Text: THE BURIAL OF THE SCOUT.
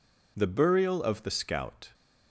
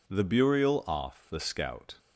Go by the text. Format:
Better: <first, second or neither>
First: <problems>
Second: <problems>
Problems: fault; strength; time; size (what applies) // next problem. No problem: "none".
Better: first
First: none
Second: says "Off" for "OF"; at 0.8 s